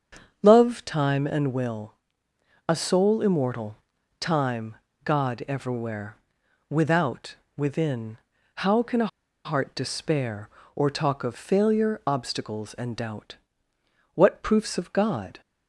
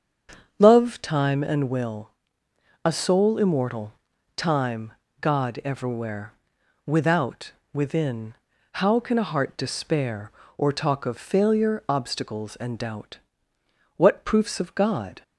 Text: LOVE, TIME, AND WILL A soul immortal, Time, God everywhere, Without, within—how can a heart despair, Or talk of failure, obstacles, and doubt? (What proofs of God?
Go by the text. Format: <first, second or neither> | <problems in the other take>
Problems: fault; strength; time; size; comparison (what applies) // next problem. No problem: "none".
second | starts louder than the rest; strong; until 1.4 s; 7 dB; strong in the second // pauses between "WILL" and "A"; noticeable; at 1.9 s; 0.72 s long; noticeable in the second // pauses between "a" and "heart"; at 9.0 s; 0.37 s long